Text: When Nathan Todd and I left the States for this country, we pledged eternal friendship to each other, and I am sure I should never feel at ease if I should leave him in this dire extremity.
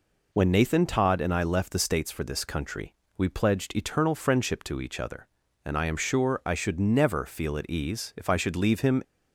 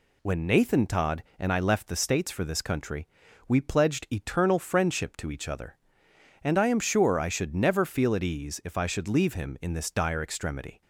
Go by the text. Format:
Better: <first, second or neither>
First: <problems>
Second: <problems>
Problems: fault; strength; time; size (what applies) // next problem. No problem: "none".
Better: second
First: stops before "in this dire extremity"; at 9.0 s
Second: none